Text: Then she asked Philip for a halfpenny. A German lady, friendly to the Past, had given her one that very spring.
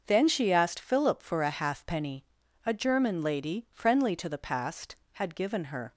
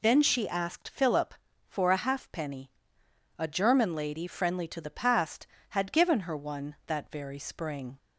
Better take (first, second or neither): second